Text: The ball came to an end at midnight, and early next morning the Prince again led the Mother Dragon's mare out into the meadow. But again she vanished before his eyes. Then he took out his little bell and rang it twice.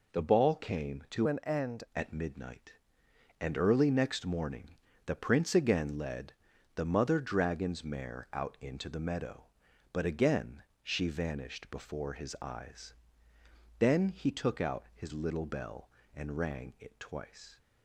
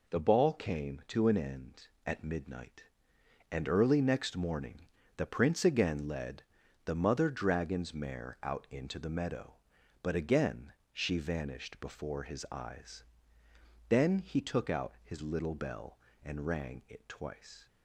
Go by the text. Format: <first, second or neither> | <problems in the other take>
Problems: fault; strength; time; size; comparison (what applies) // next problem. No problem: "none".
second | changes voice from "an" to "end"; from 1.2 to 1.8 s; 0.6 s long // pauses between "morning" and "the"; slight; at 4.7 s; 0.30 s long; slight in the second // pauses between "led" and "the"; at 6.3 s; 0.40 s long; also in the second // pauses between "again" and "she"; slight; at 10.6 s; 0.20 s long; slight in the second